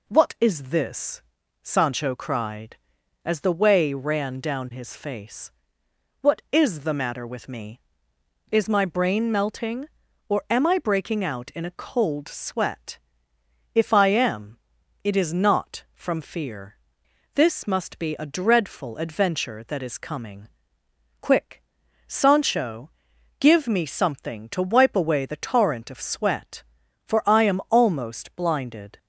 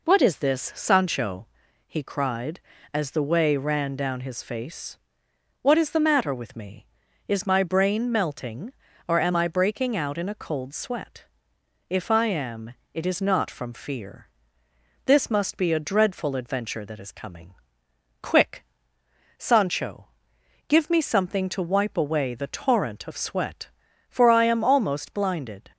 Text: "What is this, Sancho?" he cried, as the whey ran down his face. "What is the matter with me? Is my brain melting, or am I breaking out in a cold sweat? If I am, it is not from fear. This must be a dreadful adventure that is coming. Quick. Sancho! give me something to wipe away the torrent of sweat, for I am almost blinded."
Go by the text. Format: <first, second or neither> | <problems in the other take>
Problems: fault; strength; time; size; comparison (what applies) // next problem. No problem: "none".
second | skips "he"; at 2.1 s